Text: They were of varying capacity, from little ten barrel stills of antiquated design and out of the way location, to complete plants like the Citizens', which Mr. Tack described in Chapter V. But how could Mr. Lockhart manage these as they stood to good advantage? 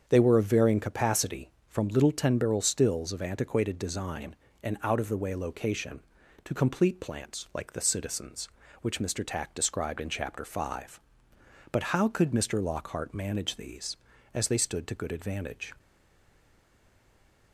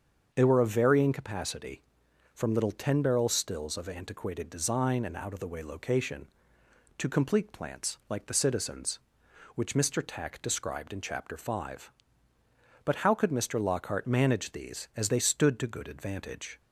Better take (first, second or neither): second